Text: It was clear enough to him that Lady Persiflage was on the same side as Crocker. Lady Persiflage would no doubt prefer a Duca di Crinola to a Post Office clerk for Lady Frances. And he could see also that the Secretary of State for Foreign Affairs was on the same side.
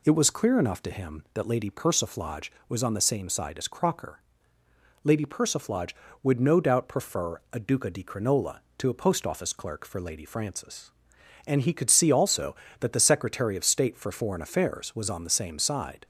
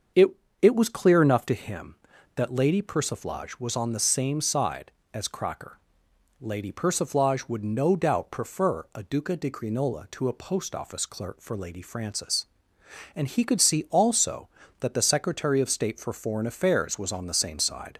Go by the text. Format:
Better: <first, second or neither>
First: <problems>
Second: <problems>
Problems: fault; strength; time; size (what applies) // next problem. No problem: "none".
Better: first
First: none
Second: starts louder than the rest; until 1.5 s; 6.5 dB // says "It" twice; at 0.6 s